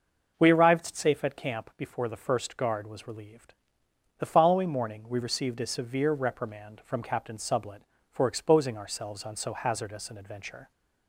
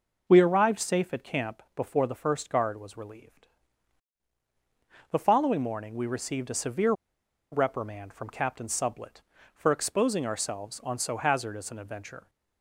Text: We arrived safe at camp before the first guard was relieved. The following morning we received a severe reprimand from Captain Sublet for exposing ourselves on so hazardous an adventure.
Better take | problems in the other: first | pauses between "severe" and "reprimand"; noticeable; at 6.9 s; 0.58 s long

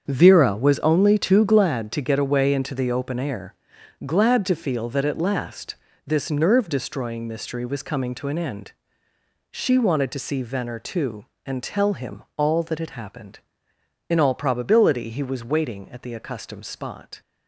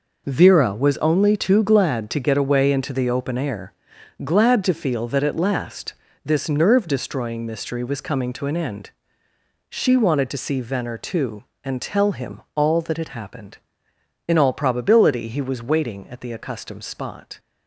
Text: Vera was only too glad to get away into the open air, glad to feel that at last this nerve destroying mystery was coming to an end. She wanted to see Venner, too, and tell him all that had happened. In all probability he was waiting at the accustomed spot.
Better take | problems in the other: second | starts louder than the rest; strong; until 1.6 s; 7 dB // pauses between "last" and "this"; slight; at 5.7 s; 0.32 s long; slight in the second

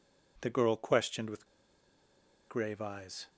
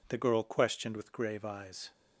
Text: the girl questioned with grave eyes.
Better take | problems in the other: second | pauses between "with" and "grave"; at 1.4 s; 1.0 s long

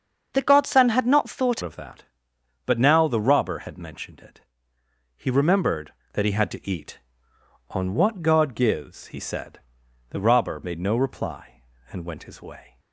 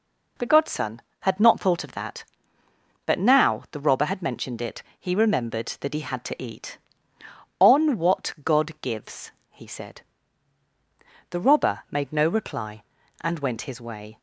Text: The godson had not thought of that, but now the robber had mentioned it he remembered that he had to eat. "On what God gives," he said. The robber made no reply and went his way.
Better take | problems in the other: second | starts louder than the rest; until 1.3 s; 7 dB // changes voice at "of"; from 1.6 s on; 11.1 s long // pauses between "it" and "he"; noticeable; at 4.4 s; 0.74 s long; slight in the second

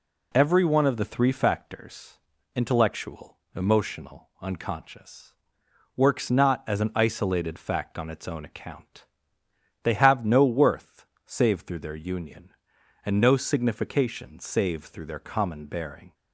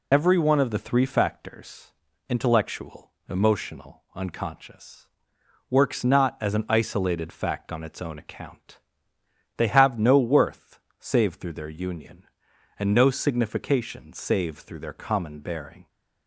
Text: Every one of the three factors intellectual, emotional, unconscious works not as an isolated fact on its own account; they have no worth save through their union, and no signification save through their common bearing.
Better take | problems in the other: first | loses the start of "Every"; at 0.1 s; 45 ms // pauses between "factors" and "intellectual"; at 1.9 s; 0.38 s long; also in the first // pauses between "unconscious" and "works"; noticeable; at 5.0 s; 0.60 s long; noticeable in the first // pauses between "worth" and "save"; slight; at 10.7 s; 0.20 s long; slight in the first

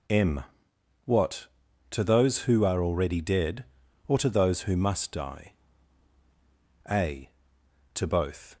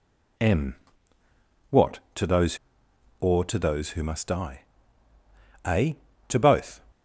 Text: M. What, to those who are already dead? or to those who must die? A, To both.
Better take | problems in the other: first | skips "who are already dead"; at 2.8 s

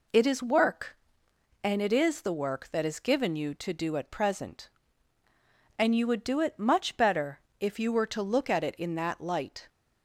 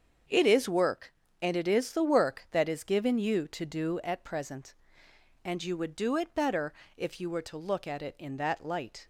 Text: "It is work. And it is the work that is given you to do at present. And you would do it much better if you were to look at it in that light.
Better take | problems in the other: first | starts louder than the rest; until 1.5 s; 7 dB // skips "much"; at 6.3 s // pauses between "better" and "if"; slight; at 6.7 s; 0.24 s long; slight in the first

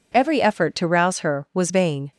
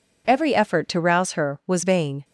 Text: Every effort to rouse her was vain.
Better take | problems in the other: neither | none

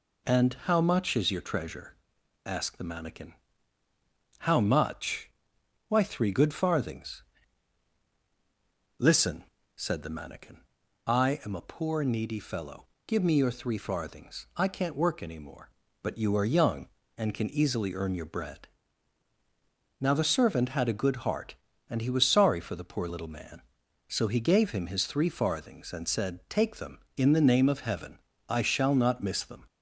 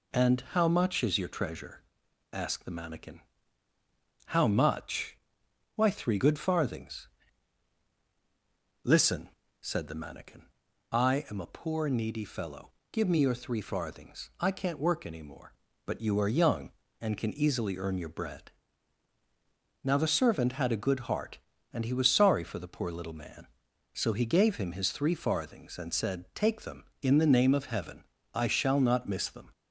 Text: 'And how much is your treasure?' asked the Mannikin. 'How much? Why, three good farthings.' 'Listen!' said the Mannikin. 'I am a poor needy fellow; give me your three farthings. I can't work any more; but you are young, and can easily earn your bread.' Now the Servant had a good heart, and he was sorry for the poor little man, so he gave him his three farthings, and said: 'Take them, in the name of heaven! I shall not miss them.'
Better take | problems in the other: neither | none

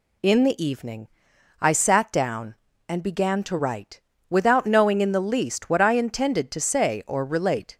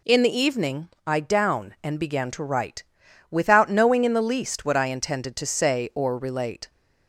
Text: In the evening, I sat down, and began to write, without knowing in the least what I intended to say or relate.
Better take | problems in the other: first | skips "sat"; at 1.2 s

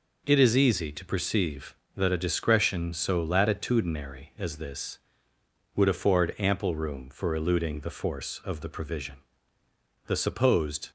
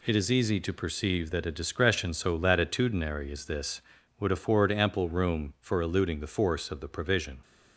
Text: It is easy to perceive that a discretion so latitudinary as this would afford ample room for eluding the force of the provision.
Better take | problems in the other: second | goes on to say "The supposed"; noticeable; from 10.0 s on; 0.86 s long

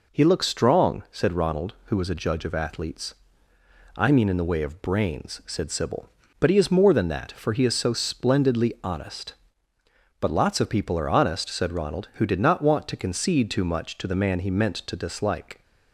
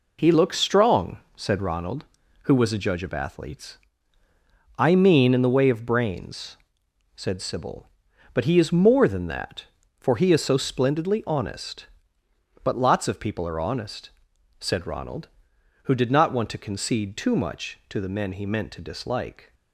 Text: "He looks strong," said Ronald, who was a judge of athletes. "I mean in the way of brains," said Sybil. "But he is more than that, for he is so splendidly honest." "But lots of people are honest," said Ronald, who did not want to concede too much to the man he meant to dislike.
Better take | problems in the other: first | says "men" for "man"; at 18.0 s

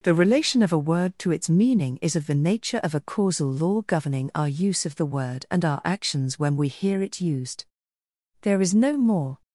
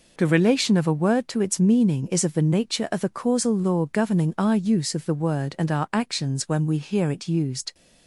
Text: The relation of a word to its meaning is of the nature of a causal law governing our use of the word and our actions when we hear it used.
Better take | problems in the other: second | goes on to say "There is no more"; noticeable; from 8.4 s on; 1.0 s long

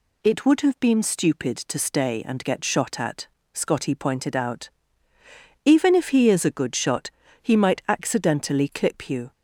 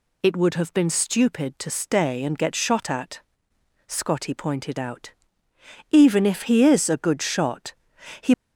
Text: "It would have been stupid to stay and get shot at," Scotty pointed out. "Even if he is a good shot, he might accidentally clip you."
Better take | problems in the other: first | stops before "might accidentally clip you"; at 8.3 s

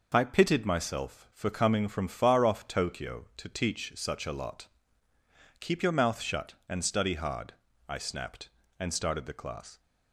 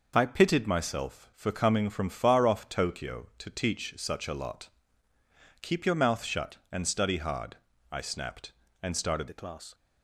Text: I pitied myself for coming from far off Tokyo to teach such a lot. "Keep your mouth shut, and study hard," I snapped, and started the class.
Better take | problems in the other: first | changes voice at "the"; from 9.2 s on; 0.5 s long

